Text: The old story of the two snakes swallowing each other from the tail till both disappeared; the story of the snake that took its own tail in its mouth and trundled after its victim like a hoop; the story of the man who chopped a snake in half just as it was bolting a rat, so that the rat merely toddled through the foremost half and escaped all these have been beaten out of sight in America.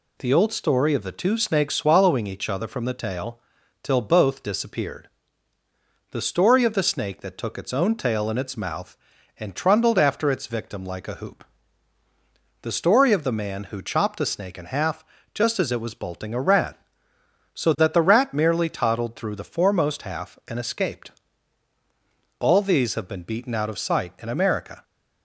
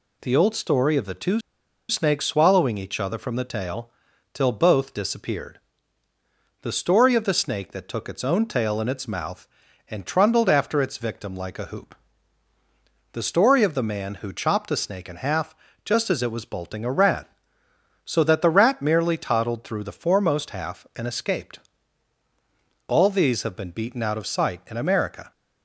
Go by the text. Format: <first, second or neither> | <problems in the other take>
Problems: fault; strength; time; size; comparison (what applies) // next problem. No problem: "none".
first | pauses between "two" and "snakes"; noticeable; at 1.4 s; 0.48 s long // pauses between "tail" and "till"; noticeable; at 3.8 s; 0.46 s long; noticeable in the first // pauses between "half" and "just"; slight; at 15.5 s; 0.30 s long; slight in the first // pauses between "escaped" and "all"; strong; at 21.5 s; 1.2 s long; strong in the first